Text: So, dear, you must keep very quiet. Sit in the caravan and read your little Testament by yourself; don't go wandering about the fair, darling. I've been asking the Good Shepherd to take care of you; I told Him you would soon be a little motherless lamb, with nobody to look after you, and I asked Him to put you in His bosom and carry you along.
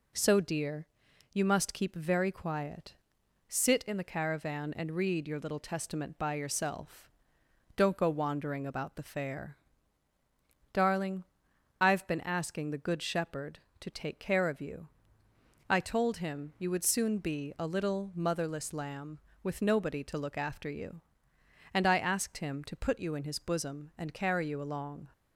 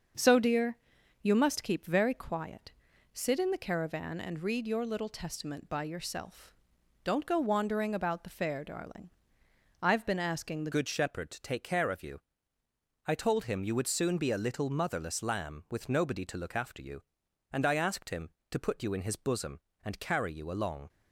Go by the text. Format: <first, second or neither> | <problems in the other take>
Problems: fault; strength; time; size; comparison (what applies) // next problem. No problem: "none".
first | starts louder than the rest; until 1.6 s; 6.5 dB // changes voice at "Good"; from 10.7 s on; 10.1 s long